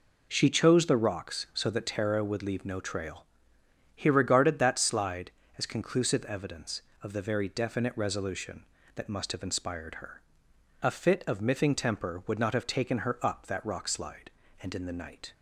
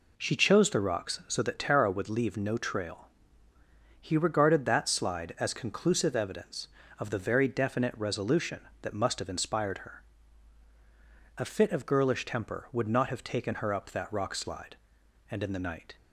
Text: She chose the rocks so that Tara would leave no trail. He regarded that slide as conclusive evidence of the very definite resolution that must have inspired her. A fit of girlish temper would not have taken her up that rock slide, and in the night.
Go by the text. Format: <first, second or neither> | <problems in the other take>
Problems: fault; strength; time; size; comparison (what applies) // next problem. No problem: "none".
second | says "miffing" for "girlish"; at 11.4 s